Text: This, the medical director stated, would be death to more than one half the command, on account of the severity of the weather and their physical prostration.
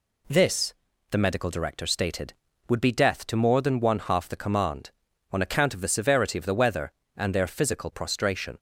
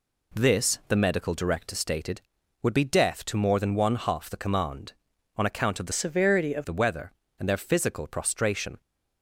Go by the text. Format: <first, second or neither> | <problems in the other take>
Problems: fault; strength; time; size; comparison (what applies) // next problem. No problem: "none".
first | changes voice from "severity" to "of"; from 5.9 to 6.6 s; 0.7 s long